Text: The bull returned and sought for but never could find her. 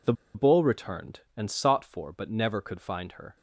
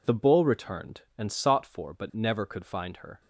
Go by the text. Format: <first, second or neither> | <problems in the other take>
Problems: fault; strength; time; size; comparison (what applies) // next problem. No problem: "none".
second | pauses between "The" and "bull"; slight; at 0.1 s; 0.22 s long